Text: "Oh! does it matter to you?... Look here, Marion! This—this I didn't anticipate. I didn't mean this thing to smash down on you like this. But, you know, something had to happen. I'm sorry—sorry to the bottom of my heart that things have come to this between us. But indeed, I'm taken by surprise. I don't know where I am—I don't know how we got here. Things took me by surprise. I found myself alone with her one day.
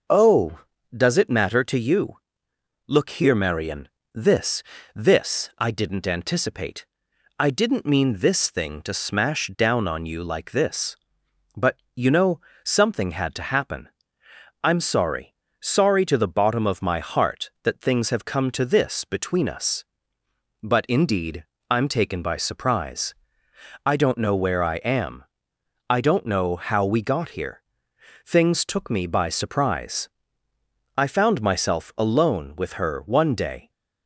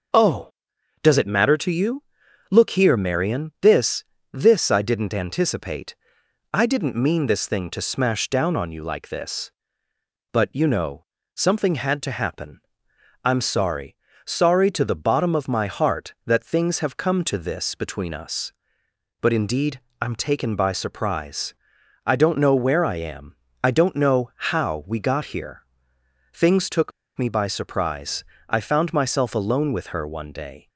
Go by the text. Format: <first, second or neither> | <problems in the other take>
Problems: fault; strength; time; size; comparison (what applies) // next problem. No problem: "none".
first | pauses between "took" and "me"; slight; at 26.9 s; 0.26 s long